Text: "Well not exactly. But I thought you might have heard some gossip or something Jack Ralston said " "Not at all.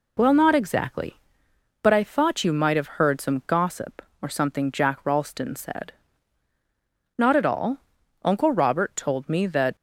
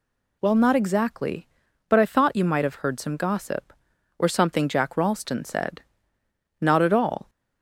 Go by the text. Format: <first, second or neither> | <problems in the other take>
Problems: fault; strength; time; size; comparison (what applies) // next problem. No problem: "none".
second | goes on to say "Uncle Robert told me that"; from 8.2 s on; 1.5 s long